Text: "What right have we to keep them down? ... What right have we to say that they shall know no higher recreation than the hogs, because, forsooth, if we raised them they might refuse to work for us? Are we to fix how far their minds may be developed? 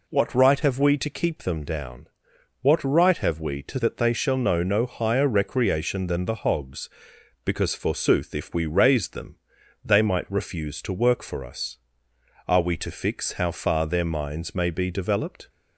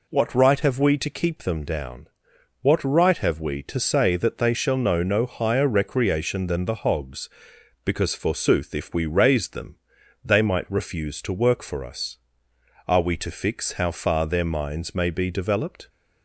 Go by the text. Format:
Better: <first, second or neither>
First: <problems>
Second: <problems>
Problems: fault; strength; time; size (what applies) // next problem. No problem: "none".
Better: second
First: skips "say"; at 3.7 s // pauses between "them" and "they"; noticeable; at 9.3 s; 0.48 s long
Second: pauses between "them" and "they"; noticeable; at 9.7 s; 0.48 s long